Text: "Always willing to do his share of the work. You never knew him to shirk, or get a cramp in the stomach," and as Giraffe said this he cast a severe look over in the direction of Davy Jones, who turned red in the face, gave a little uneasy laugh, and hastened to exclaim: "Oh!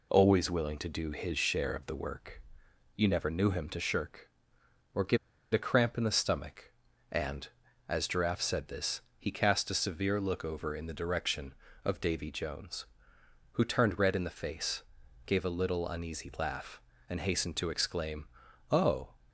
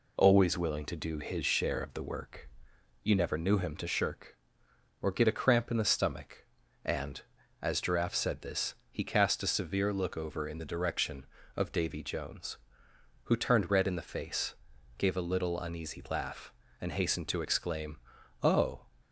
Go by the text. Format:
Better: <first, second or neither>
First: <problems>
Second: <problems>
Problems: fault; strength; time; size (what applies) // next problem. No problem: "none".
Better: second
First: pauses between "get" and "a"; at 5.1 s; 0.36 s long // pauses between "this" and "he"; slight; at 9.0 s; 0.18 s long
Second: pauses between "this" and "he"; slight; at 8.7 s; 0.19 s long